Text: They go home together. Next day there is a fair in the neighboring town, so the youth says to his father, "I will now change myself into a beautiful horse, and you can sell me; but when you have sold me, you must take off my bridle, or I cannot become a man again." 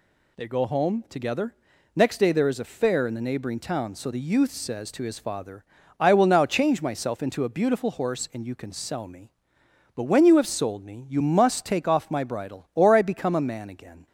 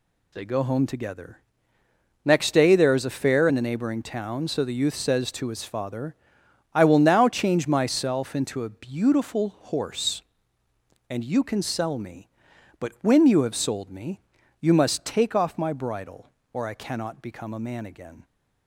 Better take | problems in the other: second | skips "cannot"; at 13.0 s

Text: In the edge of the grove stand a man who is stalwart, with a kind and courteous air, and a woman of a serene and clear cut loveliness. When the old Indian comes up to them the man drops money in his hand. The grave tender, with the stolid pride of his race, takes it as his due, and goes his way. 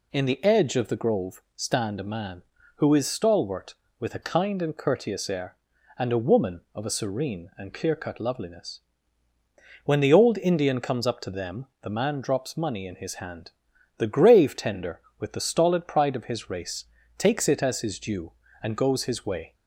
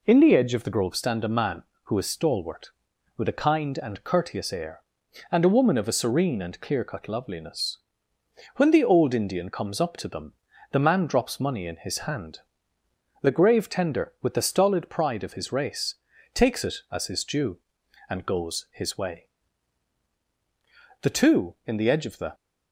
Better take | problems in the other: first | pauses between "them" and "the"; at 10.3 s; 0.40 s long; slight in the first // goes on to say "The two in the edge of the"; from 21.0 s on; 1.3 s long

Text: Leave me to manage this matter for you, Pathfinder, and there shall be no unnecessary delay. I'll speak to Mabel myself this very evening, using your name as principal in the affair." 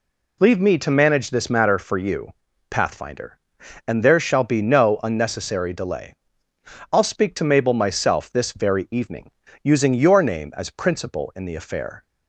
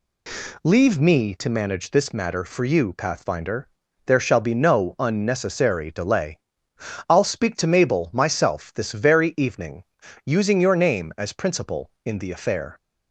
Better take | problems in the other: first | skips "and"; at 3.8 s

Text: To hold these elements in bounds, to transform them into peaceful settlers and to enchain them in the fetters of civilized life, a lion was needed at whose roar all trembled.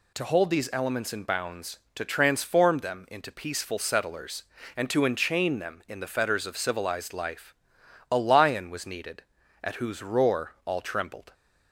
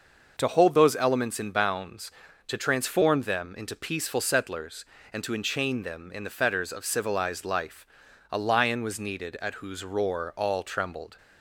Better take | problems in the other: first | says "those" for "these"; at 0.7 s

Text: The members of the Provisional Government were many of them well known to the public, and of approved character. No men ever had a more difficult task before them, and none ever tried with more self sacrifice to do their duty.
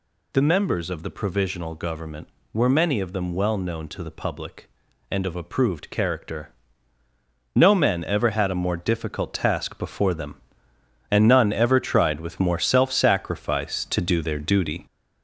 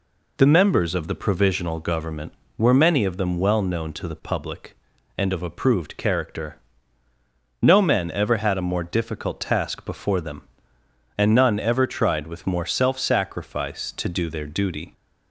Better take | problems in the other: second | gets louder; noticeable; throughout; 4 dB

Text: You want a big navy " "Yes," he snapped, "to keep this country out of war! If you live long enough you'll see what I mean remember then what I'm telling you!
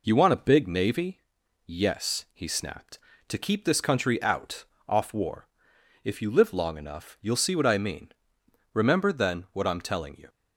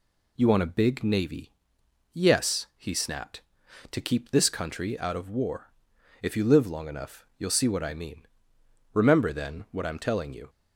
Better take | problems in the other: second | says "off" for "of"; at 4.8 s // pauses between "mean" and "remember"; noticeable; at 8.0 s; 0.66 s long; noticeable in the second

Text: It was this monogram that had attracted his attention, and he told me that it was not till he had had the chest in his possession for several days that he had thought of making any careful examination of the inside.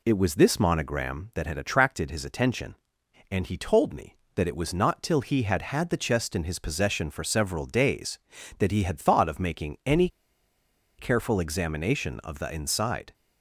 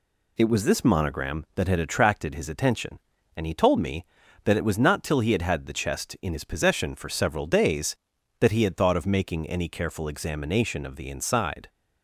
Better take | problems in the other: second | pauses between "any" and "careful"; noticeable; at 10.0 s; 0.90 s long

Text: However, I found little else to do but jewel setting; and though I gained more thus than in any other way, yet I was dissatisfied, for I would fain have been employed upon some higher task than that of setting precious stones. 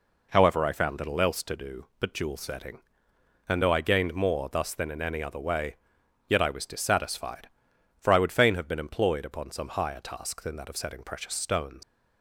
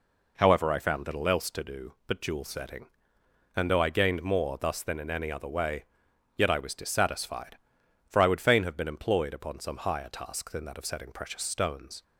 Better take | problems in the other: second | leaves "stones" unfinished; at 11.8 s; 110 ms

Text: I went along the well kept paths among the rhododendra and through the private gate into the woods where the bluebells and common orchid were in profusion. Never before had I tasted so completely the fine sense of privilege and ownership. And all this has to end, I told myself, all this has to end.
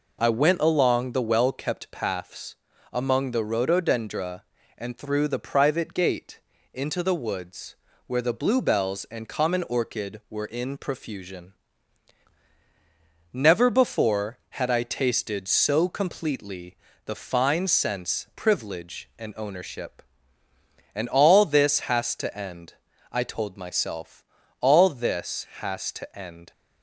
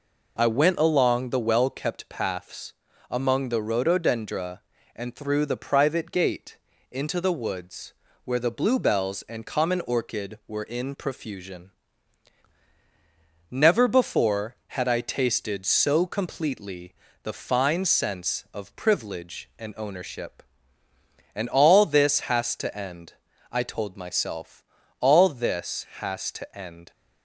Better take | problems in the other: second | pauses between "paths" and "among"; slight; at 2.5 s; 0.36 s long; slight in the second // pauses between "gate" and "into"; slight; at 6.3 s; 0.34 s long; slight in the second // pauses between "woods" and "where"; slight; at 7.7 s; 0.30 s long; slight in the second // pauses between "completely" and "the"; slight; at 16.7 s; 0.30 s long; slight in the second // skips "of"; at 18.3 s

